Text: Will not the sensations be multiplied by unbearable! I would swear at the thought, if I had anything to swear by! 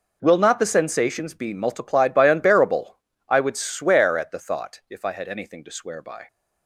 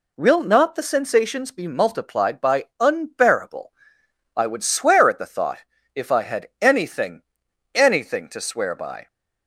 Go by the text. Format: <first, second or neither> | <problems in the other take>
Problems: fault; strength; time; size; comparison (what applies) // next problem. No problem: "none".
first | says "anything" twice; at 7.7 s